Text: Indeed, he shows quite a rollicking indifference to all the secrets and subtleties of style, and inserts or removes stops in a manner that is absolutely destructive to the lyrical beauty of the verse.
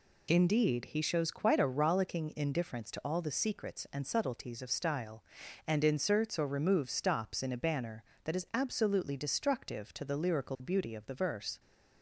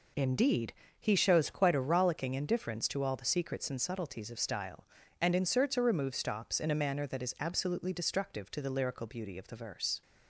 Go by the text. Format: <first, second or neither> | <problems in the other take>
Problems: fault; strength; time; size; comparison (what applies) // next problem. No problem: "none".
second | says "banner" for "manner"; at 7.5 s